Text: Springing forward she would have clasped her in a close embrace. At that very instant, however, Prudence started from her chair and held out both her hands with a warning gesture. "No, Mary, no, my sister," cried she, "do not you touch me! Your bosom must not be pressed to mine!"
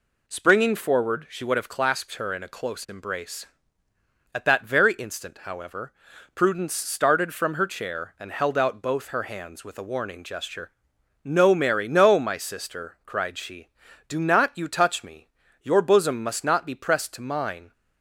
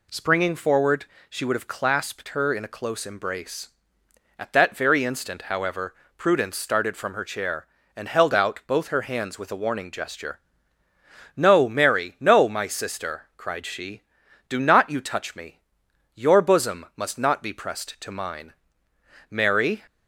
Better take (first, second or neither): first